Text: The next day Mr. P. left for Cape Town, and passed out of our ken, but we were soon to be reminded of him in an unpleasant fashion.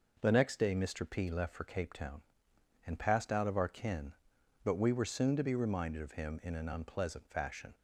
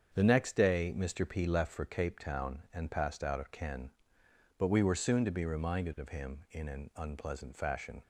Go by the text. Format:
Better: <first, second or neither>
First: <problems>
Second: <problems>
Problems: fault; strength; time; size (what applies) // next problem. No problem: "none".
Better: first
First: none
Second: starts louder than the rest; strong; until 1.1 s; 7 dB // skips "our"; at 3.5 s